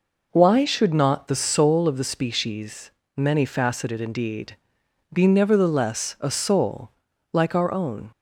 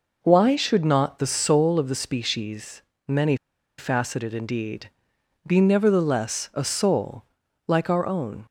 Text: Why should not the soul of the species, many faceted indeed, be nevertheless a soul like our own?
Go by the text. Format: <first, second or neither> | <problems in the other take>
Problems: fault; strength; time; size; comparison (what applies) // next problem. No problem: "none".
first | pauses between "many" and "faceted"; at 3.3 s; 0.43 s long // pauses between "soul" and "like"; at 7.2 s; 0.42 s long; also in the first